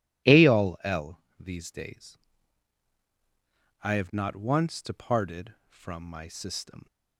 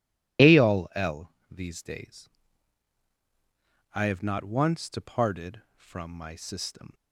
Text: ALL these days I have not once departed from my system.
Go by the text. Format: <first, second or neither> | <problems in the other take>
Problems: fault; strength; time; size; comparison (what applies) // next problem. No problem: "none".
first | loses the start of "ALL"; at 0.3 s; 30 ms // pauses between "ALL" and "these"; slight; at 1.2 s; 0.20 s long; slight in the first // pauses between "days" and "I"; strong; at 2.2 s; 1.6 s long; strong in the first